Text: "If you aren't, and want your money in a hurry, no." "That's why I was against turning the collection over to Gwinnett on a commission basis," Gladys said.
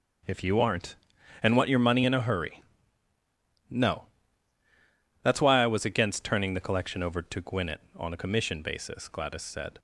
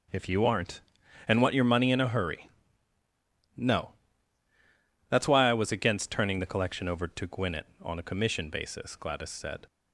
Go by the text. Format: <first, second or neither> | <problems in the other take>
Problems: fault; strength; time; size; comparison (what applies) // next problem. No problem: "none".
neither | none